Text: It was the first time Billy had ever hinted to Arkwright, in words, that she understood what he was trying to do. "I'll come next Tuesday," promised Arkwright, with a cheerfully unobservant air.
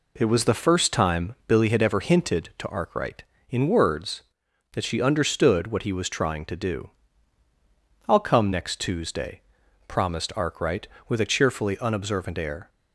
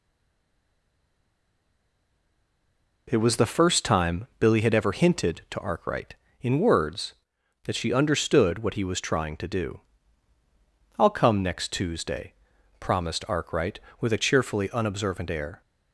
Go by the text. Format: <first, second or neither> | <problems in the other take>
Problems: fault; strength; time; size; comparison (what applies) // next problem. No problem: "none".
first | stays silent before the first word; strong; until 3.0 s; 3.0 s long